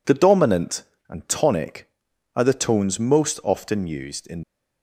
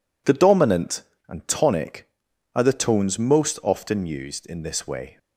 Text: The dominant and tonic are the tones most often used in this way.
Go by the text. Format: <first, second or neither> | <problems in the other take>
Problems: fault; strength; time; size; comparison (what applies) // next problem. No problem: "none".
second | stops before "this way"; at 4.4 s